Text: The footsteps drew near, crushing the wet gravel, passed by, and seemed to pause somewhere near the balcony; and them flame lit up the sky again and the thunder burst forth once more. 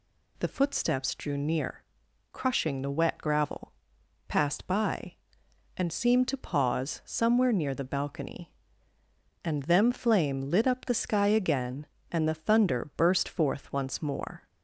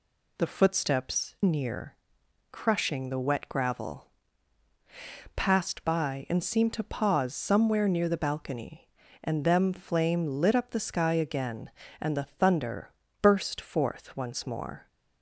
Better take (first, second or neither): first